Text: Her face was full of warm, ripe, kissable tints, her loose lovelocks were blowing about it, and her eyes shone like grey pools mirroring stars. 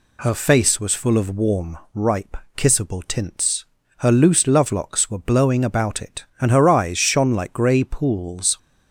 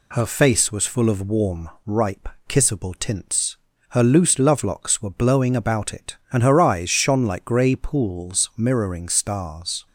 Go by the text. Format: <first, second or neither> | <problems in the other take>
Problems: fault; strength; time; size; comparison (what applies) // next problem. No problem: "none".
second | stops before "mirroring stars"; at 8.5 s